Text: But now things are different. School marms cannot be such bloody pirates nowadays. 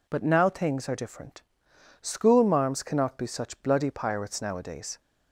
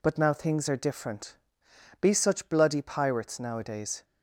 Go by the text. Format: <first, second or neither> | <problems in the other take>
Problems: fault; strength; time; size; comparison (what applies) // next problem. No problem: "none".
first | skips "School marms cannot"; at 1.6 s